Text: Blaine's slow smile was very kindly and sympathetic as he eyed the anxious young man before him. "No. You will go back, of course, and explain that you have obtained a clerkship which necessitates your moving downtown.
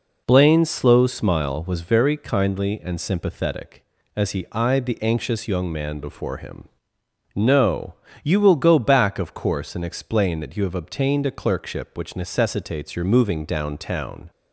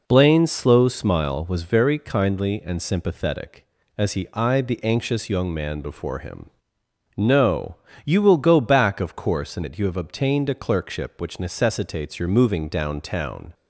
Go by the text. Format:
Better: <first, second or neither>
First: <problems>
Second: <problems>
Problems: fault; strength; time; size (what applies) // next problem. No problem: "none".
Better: first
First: none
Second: skips "explain"; at 9.6 s